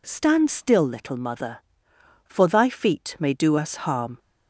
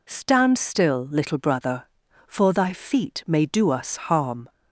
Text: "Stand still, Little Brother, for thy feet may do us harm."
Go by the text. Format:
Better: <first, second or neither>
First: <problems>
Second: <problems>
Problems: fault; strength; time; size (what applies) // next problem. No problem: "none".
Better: second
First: says "Mother" for "Brother"; at 1.1 s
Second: none